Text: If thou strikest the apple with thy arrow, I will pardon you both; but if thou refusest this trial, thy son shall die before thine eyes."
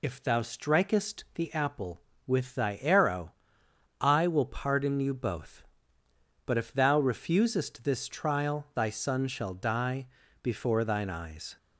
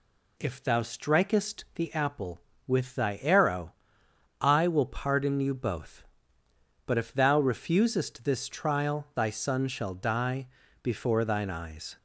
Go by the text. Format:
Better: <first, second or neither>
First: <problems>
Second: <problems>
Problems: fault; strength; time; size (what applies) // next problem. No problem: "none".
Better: second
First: loses the start of "If"; at 0.0 s; 45 ms // pauses between "die" and "before"; at 10.0 s; 0.38 s long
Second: pauses between "die" and "before"; at 10.4 s; 0.38 s long